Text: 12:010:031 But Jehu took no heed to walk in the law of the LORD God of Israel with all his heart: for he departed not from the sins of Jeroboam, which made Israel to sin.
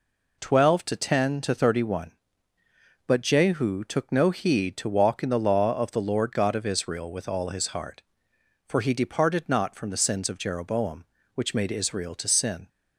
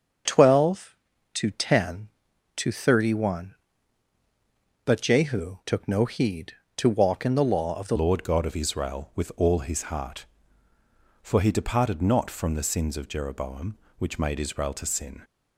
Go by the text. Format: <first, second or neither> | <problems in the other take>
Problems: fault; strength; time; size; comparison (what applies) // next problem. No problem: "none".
first | starts louder than the rest; until 1.6 s; 6.5 dB // changes voice at "LORD"; from 7.9 s on; 7.3 s long